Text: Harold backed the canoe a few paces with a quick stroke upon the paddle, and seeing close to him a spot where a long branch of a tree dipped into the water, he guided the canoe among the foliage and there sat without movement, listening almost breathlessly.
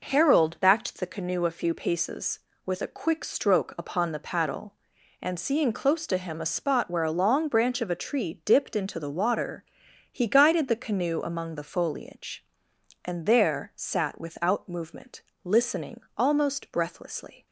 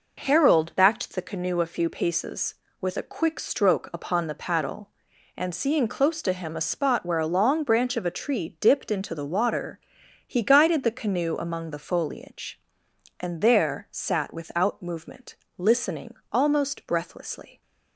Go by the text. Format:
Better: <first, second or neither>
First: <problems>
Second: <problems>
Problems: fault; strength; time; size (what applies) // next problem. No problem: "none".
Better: neither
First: pauses between "listening" and "almost"; slight; at 15.9 s; 0.16 s long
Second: pauses between "listening" and "almost"; slight; at 16.1 s; 0.18 s long